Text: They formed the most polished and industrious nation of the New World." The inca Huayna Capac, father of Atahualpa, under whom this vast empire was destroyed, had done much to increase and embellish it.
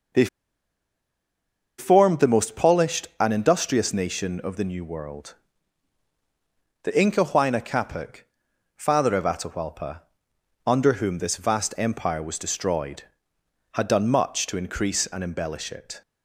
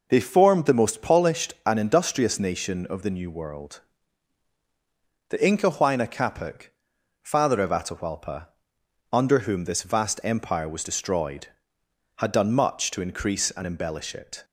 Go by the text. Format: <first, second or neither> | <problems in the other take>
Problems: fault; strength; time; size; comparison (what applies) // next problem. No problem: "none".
second | pauses between "They" and "formed"; strong; at 0.2 s; 1.5 s long